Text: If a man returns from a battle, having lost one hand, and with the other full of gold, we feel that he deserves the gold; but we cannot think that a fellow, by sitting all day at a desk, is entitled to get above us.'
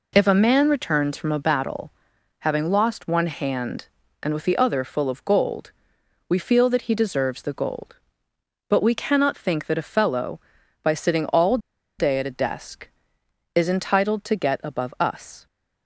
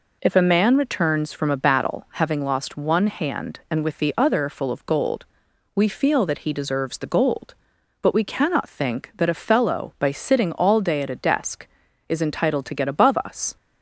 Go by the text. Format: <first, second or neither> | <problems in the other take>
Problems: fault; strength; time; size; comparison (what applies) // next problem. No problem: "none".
second | pauses between "all" and "day"; at 11.5 s; 0.40 s long